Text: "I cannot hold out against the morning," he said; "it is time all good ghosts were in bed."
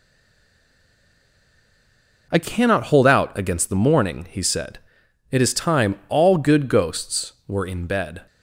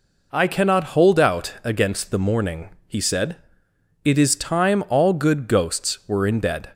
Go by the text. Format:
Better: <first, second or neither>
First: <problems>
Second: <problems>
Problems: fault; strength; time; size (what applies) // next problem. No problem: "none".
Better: second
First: stays silent before the first word; until 2.2 s; 2.2 s long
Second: none